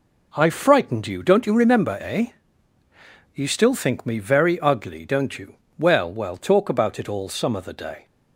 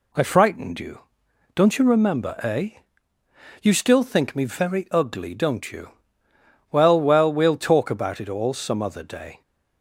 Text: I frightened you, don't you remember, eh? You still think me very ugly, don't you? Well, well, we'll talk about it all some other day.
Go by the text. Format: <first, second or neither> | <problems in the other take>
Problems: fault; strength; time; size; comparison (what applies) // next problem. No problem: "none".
second | skips "we'll"; at 6.3 s